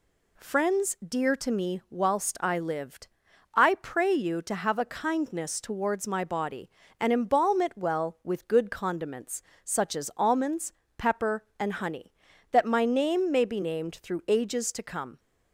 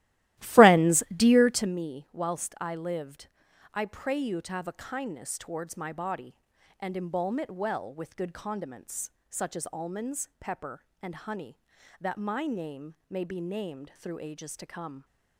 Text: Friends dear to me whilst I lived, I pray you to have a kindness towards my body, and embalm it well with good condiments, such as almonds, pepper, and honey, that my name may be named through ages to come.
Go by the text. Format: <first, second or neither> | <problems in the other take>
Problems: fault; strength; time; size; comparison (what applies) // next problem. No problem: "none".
first | starts louder than the rest; strong; until 1.8 s; 15.5 dB